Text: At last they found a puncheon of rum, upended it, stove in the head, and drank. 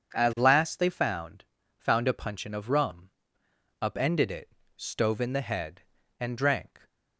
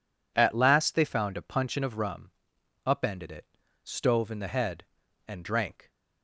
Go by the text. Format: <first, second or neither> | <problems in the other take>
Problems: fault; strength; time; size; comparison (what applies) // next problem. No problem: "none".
second | says "found" twice; at 1.7 s